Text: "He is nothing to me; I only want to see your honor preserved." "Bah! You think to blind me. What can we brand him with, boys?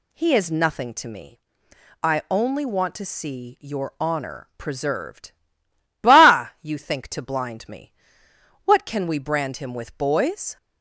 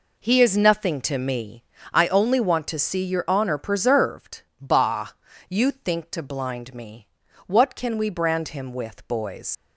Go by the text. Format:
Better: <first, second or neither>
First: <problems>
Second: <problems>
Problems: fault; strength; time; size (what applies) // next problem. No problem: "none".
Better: first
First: none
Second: leaves "boys" unfinished; at 9.5 s; 100 ms